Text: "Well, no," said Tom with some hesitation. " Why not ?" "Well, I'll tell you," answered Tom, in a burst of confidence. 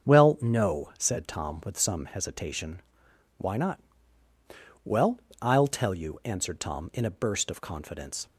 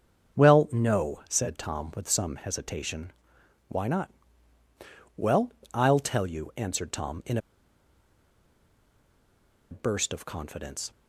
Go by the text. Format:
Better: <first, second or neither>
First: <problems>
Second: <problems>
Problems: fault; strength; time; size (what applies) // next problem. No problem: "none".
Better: first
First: starts louder than the rest; strong; until 1.1 s; 7.5 dB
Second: starts louder than the rest; strong; until 1.4 s; 7.5 dB // pauses between "in" and "a"; strong; at 7.3 s; 2.3 s long